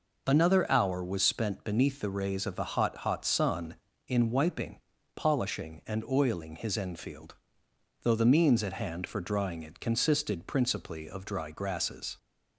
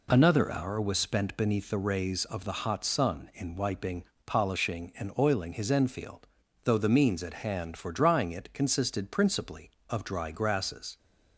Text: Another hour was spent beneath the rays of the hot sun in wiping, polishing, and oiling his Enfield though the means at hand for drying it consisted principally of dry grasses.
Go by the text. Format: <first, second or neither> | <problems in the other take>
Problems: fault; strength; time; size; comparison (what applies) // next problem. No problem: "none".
second | says "hot" twice; at 2.9 s // pauses between "Enfield" and "though"; noticeable; at 7.3 s; 0.70 s long; also in the second